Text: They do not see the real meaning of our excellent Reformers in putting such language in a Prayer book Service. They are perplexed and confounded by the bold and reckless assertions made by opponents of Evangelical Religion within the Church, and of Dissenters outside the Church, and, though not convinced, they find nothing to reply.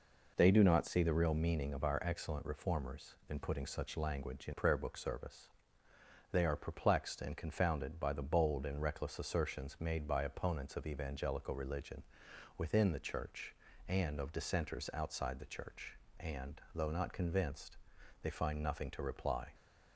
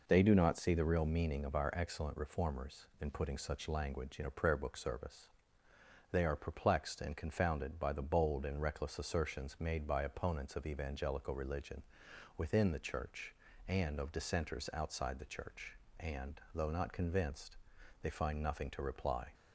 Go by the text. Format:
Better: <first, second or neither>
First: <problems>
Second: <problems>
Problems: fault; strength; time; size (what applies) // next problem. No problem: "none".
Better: second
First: skips "a"; at 4.5 s // pauses between "Religion" and "within"; noticeable; at 12.0 s; 0.52 s long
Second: pauses between "Religion" and "within"; noticeable; at 11.8 s; 0.52 s long